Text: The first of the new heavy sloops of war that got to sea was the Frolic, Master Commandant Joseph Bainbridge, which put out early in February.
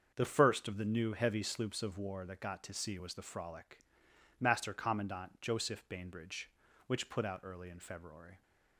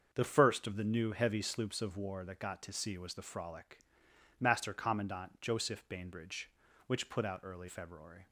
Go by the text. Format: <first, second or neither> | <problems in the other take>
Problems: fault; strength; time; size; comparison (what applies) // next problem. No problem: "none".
first | starts louder than the rest; until 1.1 s; 6.5 dB; also in the first // skips "in"; at 7.6 s